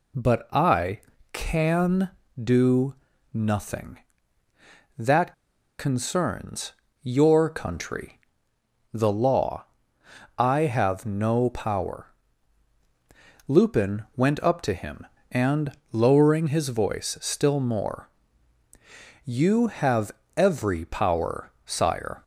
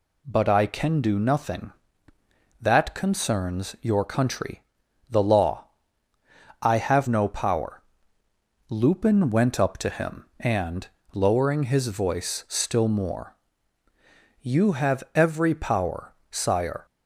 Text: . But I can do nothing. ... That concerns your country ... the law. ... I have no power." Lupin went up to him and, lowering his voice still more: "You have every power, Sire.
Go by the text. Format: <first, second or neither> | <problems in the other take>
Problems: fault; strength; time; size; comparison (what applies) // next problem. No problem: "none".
second | pauses between "do" and "nothing"; at 2.9 s; 0.38 s long // pauses between "That" and "concerns"; at 5.3 s; 0.44 s long // pauses between "concerns" and "your"; slight; at 6.7 s; 0.28 s long // pauses between "have" and "every"; slight; at 20.1 s; 0.24 s long